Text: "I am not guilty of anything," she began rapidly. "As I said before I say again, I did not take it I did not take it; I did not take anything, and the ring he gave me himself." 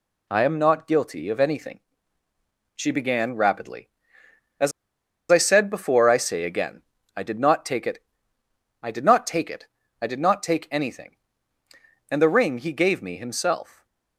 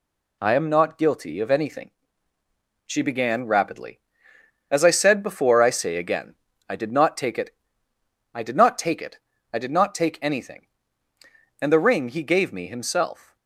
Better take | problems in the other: second | pauses between "As" and "I"; noticeable; at 4.7 s; 0.60 s long // pauses between "it" and "I"; noticeable; at 8.0 s; 0.78 s long; noticeable in the second // stays silent after the last word; slight; from 13.6 s on; 0.5 s long

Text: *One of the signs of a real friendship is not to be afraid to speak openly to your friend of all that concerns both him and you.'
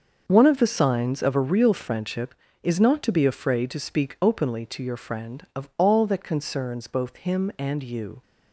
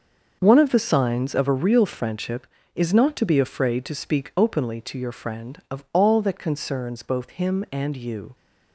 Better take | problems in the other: neither | starts louder than the rest; the same in both

